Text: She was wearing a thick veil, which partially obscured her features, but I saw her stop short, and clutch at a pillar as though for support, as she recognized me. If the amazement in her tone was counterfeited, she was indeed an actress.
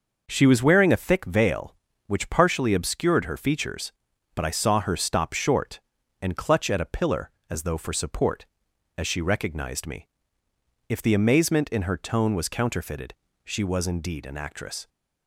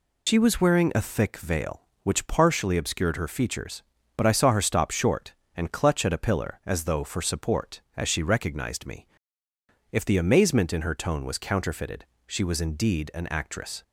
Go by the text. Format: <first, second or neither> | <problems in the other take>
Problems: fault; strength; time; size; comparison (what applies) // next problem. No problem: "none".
first | loses the start of "She"; at 0.2 s; 100 ms